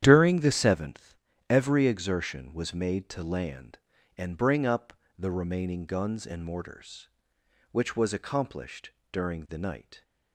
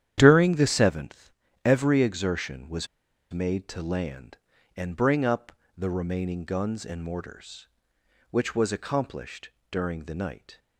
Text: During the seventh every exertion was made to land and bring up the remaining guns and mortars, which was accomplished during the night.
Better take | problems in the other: first | starts louder than the rest; strong; until 1.1 s; 10 dB; strong in the first // pauses between "seventh" and "every"; slight; at 1.3 s; 0.34 s long; slight in the first // pauses between "was" and "made"; at 2.8 s; 0.45 s long // pauses between "up" and "the"; slight; at 5.5 s; 0.26 s long; slight in the first // pauses between "accomplished" and "during"; slight; at 9.4 s; 0.22 s long; slight in the first

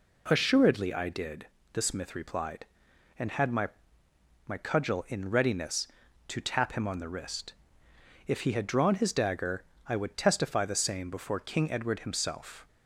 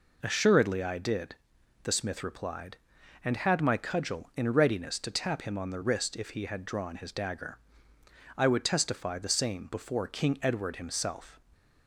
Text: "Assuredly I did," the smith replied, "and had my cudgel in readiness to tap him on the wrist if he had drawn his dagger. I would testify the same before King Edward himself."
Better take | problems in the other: second | says "my" twice; at 4.4 s // pauses between "wrist" and "if"; noticeable; at 7.5 s; 0.74 s long

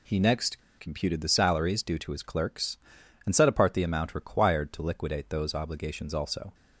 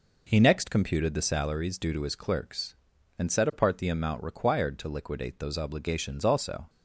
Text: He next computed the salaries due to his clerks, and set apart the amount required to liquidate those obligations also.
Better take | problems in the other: second | pauses between "next" and "computed"; slight; at 0.6 s; 0.19 s long

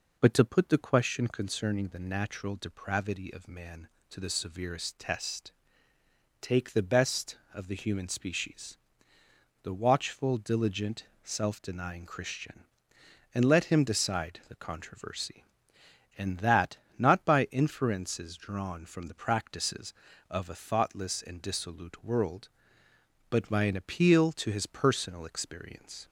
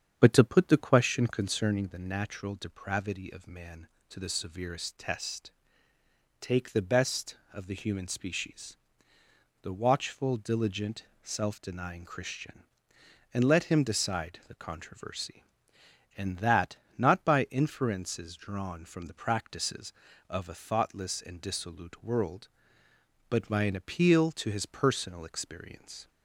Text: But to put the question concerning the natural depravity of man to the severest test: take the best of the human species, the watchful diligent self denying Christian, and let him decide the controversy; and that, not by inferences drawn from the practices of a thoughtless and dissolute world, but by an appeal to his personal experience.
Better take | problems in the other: first | starts louder than the rest; strong; until 2.0 s; 8 dB // pauses between "diligent" and "self"; slight; at 11.0 s; 0.18 s long; slight in the first

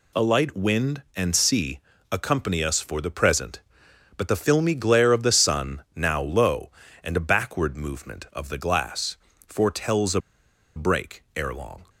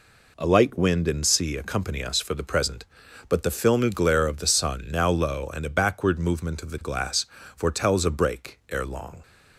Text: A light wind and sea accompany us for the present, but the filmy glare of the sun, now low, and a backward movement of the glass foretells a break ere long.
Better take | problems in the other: second | pauses between "sea" and "accompany"; slight; at 1.7 s; 0.32 s long // pauses between "glass" and "foretells"; slight; at 9.1 s; 0.32 s long; slight in the second // pauses between "a" and "break"; noticeable; at 10.1 s; 0.55 s long

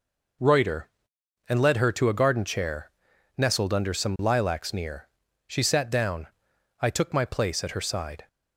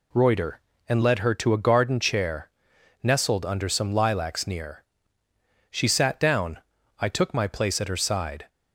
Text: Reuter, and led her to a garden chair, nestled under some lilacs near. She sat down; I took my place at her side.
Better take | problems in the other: neither | none

